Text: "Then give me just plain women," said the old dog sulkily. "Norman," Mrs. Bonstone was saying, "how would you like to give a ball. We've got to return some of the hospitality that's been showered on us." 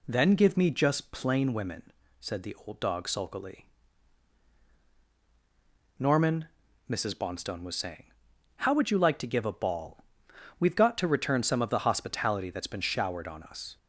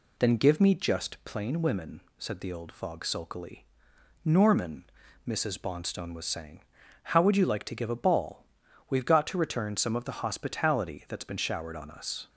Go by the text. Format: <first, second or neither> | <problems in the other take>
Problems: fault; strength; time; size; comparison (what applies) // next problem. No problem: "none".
first | says "fog" for "dog"; at 2.7 s